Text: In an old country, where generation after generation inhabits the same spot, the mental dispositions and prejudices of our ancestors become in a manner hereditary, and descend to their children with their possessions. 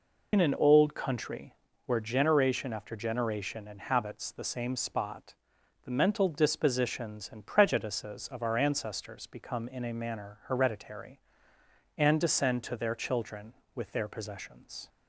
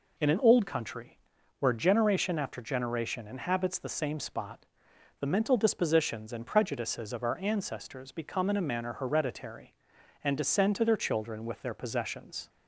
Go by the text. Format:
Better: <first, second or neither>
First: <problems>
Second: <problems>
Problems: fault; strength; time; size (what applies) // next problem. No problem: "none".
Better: second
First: loses the start of "In"; at 0.3 s; 65 ms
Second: none